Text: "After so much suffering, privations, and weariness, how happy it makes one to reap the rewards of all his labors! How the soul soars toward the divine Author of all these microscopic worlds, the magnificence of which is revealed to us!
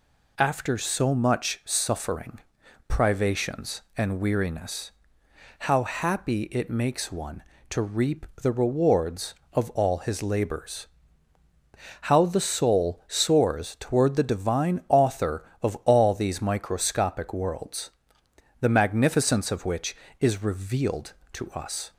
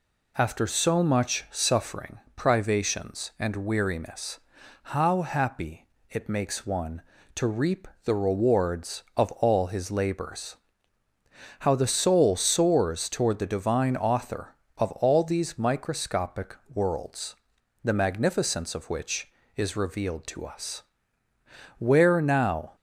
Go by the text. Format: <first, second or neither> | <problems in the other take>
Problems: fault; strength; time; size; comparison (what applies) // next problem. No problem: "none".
first | pauses between "happy" and "it"; slight; at 5.8 s; 0.22 s long // pauses between "reap" and "the"; slight; at 7.8 s; 0.18 s long; slight in the first // pauses between "microscopic" and "worlds"; slight; at 16.5 s; 0.18 s long // goes on to say "Where now"; noticeable; from 21.7 s on; 0.98 s long